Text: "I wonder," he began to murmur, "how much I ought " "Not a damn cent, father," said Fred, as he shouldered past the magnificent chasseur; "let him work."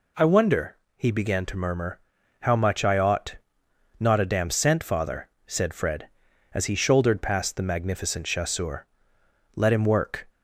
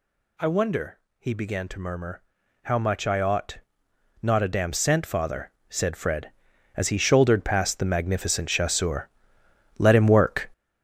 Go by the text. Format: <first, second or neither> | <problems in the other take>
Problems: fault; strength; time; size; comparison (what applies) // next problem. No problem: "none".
first | gets louder; strong; throughout; 10 dB